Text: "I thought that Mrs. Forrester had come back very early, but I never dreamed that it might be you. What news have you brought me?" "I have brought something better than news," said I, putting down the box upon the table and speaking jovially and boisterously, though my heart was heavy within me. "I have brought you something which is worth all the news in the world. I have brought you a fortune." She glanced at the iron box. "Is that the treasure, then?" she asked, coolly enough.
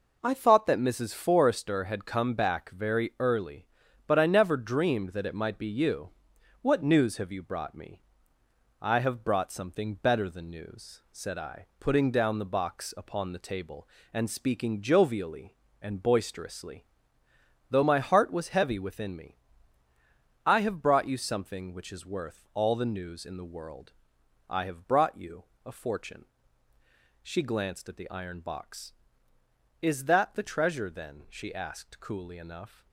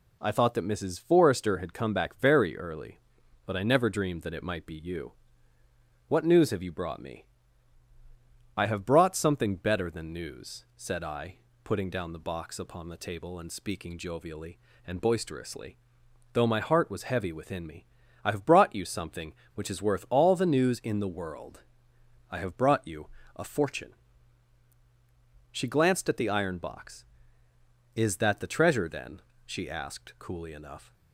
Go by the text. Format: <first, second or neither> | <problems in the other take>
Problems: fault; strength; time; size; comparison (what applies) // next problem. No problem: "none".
neither | pauses between "you" and "a"; slight; the same in both